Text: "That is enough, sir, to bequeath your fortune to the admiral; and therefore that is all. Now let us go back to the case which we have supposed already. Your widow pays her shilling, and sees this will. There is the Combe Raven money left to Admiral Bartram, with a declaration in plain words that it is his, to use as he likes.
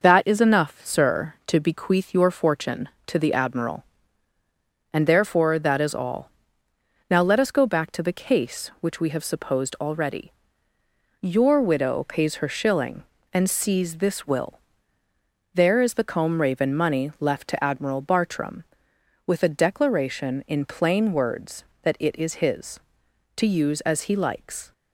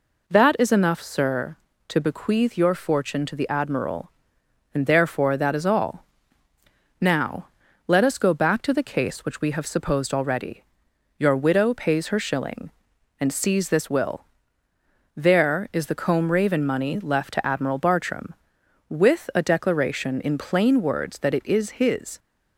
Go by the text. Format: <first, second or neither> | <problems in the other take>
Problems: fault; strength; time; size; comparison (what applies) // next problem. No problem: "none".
first | pauses between "Now" and "let"; at 7.4 s; 0.40 s long // stops before "to use as he likes"; at 22.1 s